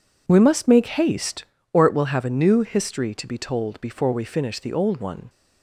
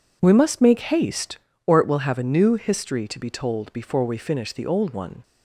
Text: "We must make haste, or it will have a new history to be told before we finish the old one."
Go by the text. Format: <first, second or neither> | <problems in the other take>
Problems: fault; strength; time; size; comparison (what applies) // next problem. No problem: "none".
neither | none